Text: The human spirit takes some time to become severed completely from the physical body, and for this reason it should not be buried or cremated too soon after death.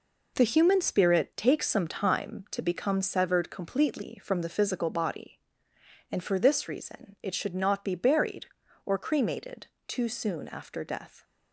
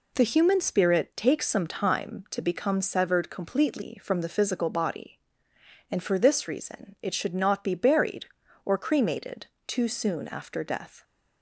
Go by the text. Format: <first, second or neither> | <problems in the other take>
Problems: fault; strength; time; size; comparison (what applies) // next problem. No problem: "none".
second | gets quieter; strong; throughout; 7.5 dB // pauses between "cremated" and "too"; slight; at 9.6 s; 0.18 s long; slight in the second